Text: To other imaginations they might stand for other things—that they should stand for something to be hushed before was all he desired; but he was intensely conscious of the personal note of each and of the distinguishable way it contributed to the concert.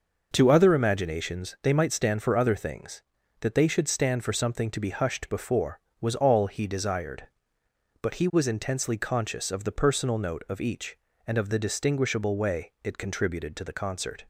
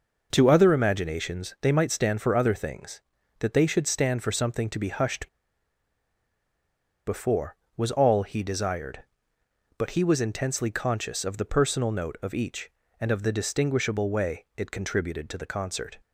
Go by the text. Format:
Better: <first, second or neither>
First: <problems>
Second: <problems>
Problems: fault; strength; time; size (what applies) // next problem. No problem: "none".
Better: first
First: none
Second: pauses between "hushed" and "before"; strong; at 5.2 s; 1.7 s long